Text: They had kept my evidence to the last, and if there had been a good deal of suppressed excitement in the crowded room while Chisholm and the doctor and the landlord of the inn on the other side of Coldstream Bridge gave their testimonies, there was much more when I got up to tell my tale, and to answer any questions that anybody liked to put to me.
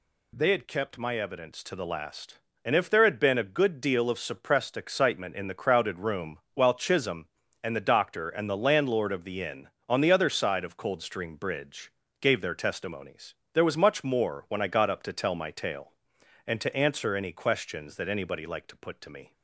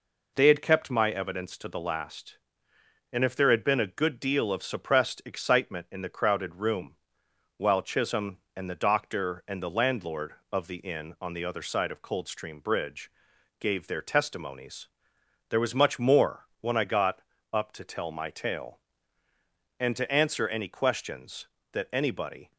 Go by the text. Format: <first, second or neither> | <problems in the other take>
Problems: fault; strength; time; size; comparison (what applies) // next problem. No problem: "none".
first | pauses between "room" and "while"; noticeable; at 6.9 s; 0.62 s long; slight in the first // pauses between "Bridge" and "gave"; noticeable; at 13.0 s; 0.52 s long; slight in the first // pauses between "got" and "up"; slight; at 17.1 s; 0.34 s long // stops before "liked to put to me"; at 22.5 s